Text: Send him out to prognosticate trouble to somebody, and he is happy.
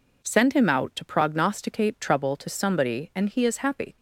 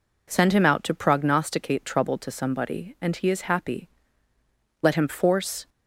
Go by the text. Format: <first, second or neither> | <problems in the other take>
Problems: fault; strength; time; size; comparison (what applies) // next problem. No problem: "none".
first | goes on to say "Let him force"; noticeable; from 4.8 s on; 0.86 s long